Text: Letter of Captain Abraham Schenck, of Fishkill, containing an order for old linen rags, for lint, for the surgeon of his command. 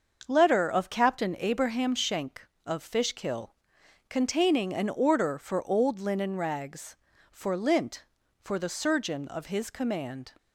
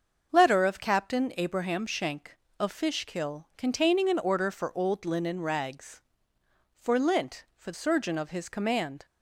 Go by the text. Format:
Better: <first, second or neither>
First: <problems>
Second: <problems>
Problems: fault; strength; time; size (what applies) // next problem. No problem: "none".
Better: first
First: starts louder than the rest; until 1.3 s; 6.5 dB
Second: starts louder than the rest; until 1.3 s; 6.5 dB // skips "the"; at 7.7 s